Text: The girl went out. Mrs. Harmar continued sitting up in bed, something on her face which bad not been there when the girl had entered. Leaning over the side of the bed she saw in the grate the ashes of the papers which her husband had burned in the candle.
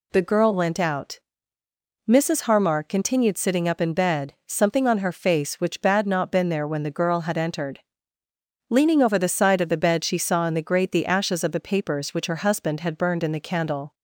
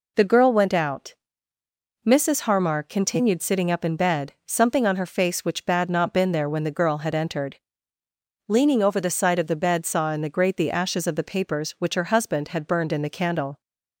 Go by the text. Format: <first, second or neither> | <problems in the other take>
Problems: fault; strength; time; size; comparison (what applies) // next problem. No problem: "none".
first | skips "she"; at 9.8 s